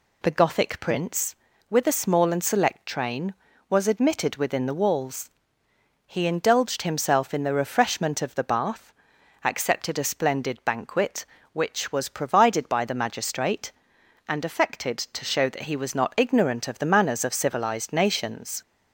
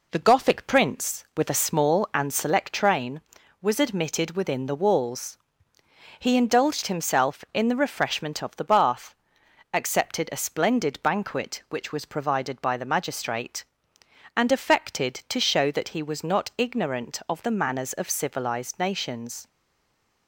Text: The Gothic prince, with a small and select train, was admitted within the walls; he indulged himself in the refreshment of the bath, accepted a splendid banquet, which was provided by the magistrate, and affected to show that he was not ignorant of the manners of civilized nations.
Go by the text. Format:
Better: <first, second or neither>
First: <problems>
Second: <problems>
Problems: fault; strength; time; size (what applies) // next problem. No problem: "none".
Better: first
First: none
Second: stays silent after the last word; slight; from 19.4 s on; 0.8 s long